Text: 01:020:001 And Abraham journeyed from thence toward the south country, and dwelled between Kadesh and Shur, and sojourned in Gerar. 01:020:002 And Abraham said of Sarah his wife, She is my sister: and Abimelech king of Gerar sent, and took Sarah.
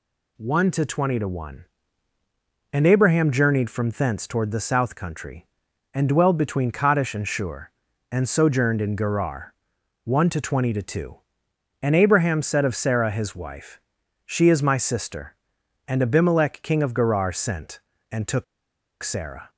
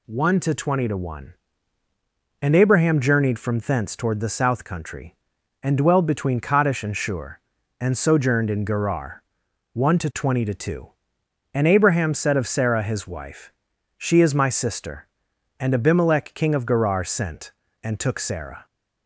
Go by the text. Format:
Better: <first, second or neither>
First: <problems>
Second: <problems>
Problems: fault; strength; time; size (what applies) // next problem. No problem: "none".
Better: second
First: pauses between "took" and "Sarah"; noticeable; at 18.4 s; 0.59 s long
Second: none